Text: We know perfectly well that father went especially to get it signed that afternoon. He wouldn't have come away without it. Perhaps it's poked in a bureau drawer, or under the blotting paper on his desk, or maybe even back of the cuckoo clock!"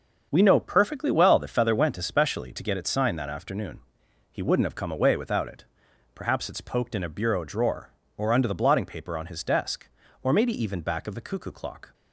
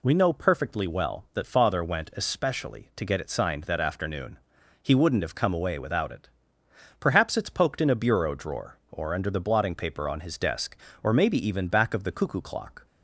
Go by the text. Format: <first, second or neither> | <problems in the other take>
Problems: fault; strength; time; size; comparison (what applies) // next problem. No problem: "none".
second | starts louder than the rest; until 1.3 s; 6.5 dB // says "feather" for "father"; at 1.4 s